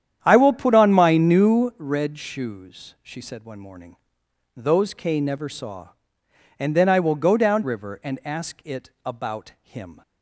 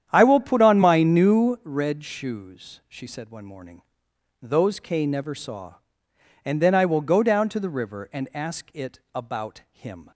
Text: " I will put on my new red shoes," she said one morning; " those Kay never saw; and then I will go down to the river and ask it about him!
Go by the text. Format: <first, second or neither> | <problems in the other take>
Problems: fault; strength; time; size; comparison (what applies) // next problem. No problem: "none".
second | starts louder than the rest; strong; until 1.2 s; 9.5 dB; strong in the second // skips "to the"; at 7.6 s